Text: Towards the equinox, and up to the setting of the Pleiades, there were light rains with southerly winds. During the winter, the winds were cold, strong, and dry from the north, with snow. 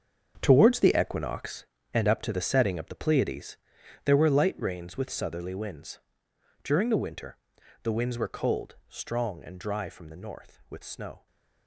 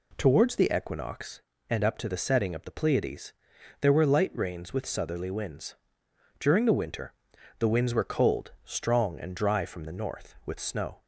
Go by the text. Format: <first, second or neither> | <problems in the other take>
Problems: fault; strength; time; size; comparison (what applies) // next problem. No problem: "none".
second | gets quieter; strong; throughout; 13 dB